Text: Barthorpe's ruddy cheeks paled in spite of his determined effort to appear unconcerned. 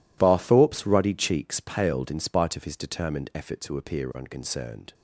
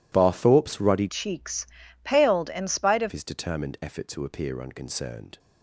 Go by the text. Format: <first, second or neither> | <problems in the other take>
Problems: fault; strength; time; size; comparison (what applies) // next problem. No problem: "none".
first | changes voice from "cheeks" to "of"; from 1.0 to 3.1 s; 2.1 s long // pauses between "cheeks" and "paled"; slight; at 1.6 s; 0.34 s long